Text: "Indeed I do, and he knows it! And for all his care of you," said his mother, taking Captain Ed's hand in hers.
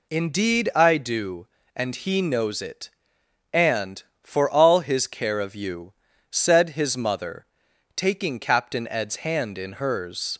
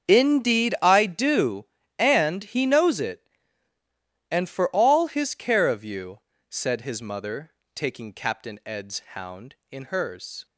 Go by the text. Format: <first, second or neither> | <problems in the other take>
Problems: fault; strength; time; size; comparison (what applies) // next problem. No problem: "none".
first | starts louder than the rest; strong; until 1.1 s; 7 dB // says "hound" for "hand"; at 9.1 s